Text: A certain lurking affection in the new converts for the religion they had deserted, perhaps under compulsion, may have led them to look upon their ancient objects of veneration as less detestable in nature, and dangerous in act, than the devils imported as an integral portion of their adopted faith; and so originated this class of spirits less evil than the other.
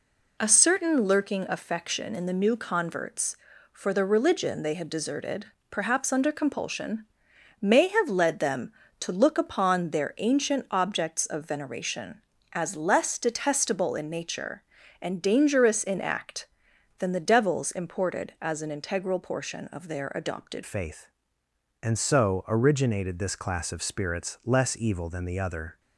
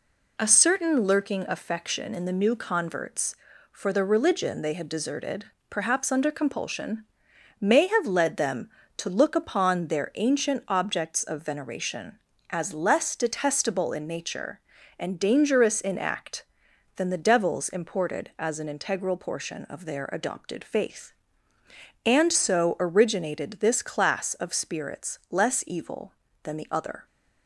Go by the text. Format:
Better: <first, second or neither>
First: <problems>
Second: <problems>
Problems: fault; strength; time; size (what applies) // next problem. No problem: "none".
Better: second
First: changes voice at "faith"; from 20.6 s on; 5.1 s long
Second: none